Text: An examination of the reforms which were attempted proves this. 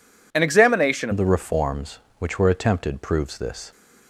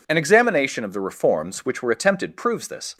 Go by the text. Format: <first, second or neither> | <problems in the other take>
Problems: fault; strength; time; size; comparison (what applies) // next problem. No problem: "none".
second | changes voice at "of"; from 1.1 s on; 2.6 s long